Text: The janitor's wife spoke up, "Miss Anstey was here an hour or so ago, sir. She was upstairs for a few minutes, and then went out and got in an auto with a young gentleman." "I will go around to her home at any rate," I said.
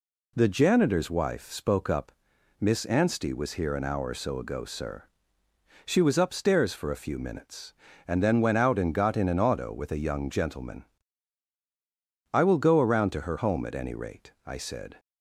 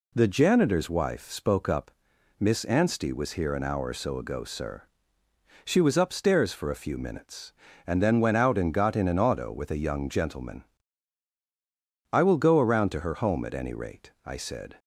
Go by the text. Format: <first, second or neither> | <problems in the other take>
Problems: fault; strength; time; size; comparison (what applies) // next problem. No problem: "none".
neither | none